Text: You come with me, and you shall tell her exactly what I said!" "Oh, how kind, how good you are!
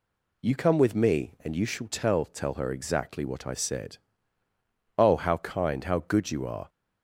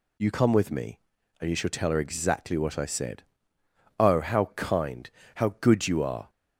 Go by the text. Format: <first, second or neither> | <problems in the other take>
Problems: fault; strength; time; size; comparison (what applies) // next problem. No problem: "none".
second | says "tell" twice; at 2.2 s